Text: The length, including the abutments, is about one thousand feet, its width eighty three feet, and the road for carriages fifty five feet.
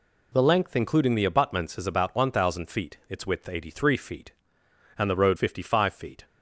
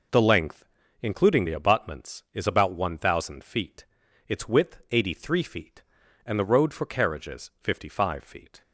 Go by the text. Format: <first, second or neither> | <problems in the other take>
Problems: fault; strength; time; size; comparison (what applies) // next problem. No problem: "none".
second | skips "for carriages"; at 5.3 s